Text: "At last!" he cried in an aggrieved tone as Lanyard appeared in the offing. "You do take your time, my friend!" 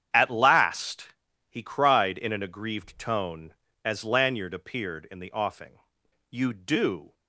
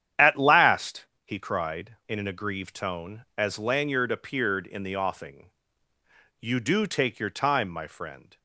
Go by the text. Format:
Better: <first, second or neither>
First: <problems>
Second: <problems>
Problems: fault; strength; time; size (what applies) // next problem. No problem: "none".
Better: second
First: starts louder than the rest; strong; until 1.5 s; 9 dB // stops before "take your time my friend"; at 7.1 s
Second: starts louder than the rest; strong; until 1.4 s; 9.5 dB